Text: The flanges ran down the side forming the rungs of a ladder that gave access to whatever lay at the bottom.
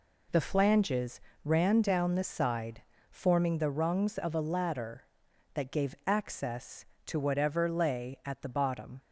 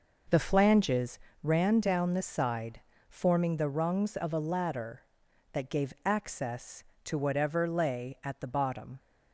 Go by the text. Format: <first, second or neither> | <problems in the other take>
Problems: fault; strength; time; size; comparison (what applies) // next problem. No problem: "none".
first | starts louder than the rest; noticeable; until 1.2 s; 5.5 dB // pauses between "flanges" and "ran"; slight; at 1.1 s; 0.24 s long; slight in the first // pauses between "side" and "forming"; slight; at 2.8 s; 0.28 s long; slight in the first